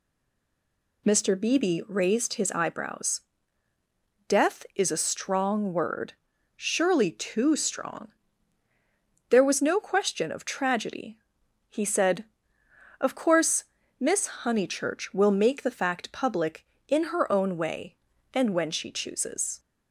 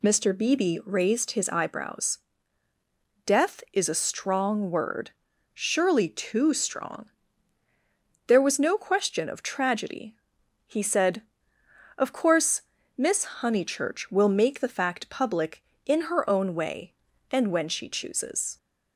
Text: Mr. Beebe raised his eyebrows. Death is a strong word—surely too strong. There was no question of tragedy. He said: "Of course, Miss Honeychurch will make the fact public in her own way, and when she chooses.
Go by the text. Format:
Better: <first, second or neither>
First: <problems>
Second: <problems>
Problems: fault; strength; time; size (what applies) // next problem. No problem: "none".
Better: second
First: stays silent before the first word; until 1.0 s; 1.0 s long // pauses between "Miss" and "Honeychurch"; slight; at 14.2 s; 0.16 s long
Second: pauses between "Miss" and "Honeychurch"; slight; at 13.2 s; 0.16 s long